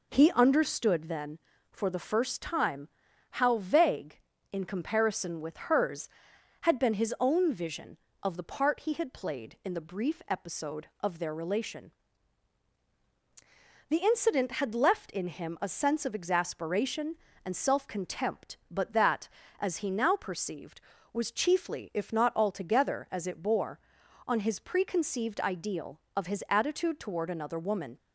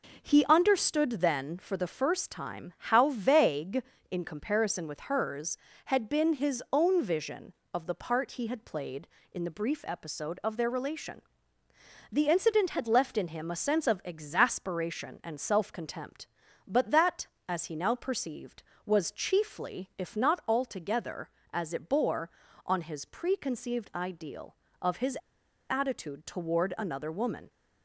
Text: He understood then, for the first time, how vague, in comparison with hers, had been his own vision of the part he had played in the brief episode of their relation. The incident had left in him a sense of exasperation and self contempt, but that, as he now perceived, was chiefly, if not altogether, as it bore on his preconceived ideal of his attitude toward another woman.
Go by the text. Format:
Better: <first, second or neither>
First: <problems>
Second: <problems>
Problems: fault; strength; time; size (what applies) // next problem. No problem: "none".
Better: first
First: none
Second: pauses between "his" and "attitude"; noticeable; at 25.1 s; 0.51 s long